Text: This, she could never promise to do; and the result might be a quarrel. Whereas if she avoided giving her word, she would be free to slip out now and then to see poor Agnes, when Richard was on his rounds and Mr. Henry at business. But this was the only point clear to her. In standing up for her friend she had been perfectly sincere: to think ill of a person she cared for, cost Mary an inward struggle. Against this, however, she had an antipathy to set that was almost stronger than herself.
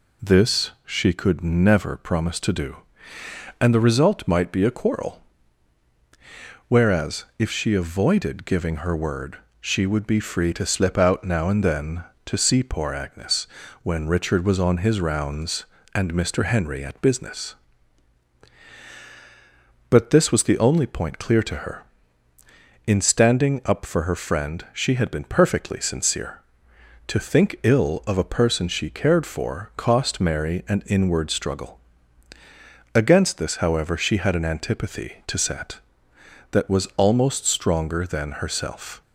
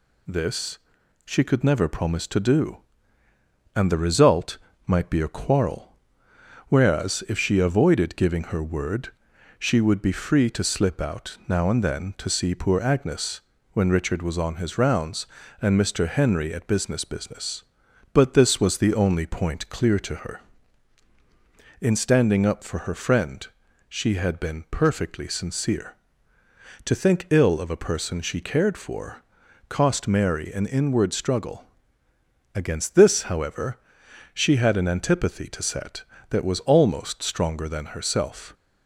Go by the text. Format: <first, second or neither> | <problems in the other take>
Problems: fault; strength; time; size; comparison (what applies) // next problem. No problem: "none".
first | pauses between "result" and "might"; slight; at 4.5 s; 0.30 s long // says "business" twice; at 17.0 s // pauses between "friend" and "she"; at 23.4 s; 0.40 s long